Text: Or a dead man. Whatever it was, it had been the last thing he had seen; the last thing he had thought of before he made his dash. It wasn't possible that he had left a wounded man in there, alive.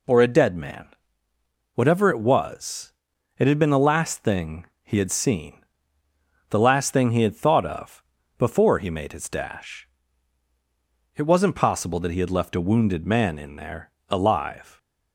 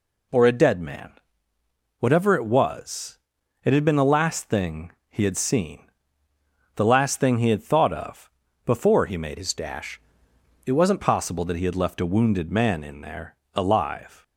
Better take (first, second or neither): first